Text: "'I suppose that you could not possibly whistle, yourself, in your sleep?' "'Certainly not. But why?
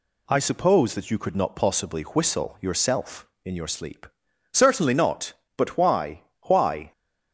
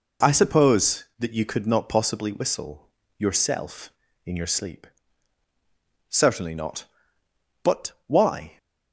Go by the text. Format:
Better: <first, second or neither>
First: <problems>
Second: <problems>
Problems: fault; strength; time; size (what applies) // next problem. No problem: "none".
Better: second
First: says "why" twice; at 6.4 s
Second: none